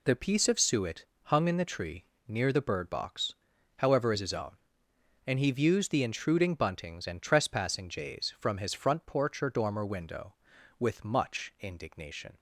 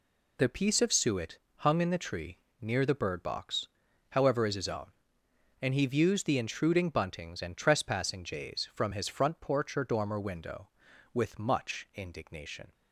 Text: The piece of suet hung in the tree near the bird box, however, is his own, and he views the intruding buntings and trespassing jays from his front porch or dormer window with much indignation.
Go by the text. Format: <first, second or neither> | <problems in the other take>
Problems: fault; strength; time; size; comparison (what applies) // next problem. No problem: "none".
neither | pauses between "suet" and "hung"; slight; the same in both // pauses between "tree" and "near"; slight; the same in both